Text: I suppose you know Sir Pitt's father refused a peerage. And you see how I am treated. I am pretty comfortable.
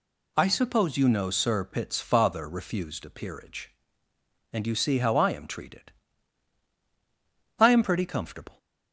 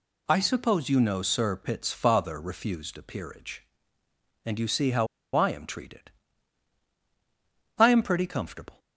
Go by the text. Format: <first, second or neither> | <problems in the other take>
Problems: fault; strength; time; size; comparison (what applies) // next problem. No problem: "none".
first | pauses between "how" and "I"; slight; at 5.0 s; 0.27 s long